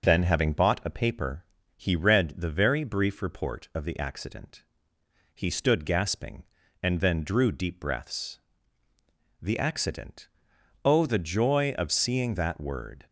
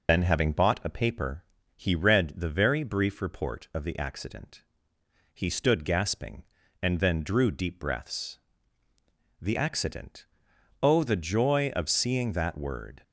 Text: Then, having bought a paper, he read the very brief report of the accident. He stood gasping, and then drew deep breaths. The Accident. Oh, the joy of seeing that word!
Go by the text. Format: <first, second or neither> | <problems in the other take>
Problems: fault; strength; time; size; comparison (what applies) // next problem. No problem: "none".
first | loses the start of "Then"; at 0.0 s; 65 ms